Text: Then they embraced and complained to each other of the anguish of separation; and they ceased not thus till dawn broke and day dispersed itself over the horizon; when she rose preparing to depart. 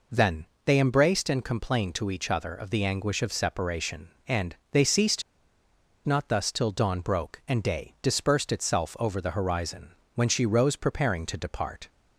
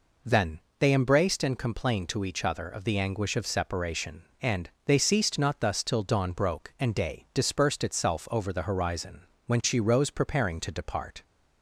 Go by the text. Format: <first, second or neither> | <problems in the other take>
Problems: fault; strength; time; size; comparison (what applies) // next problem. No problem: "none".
second | pauses between "Then" and "they"; slight; at 0.4 s; 0.20 s long; slight in the second // pauses between "and" and "they"; slight; at 4.5 s; 0.16 s long; slight in the second // pauses between "ceased" and "not"; noticeable; at 5.2 s; 0.84 s long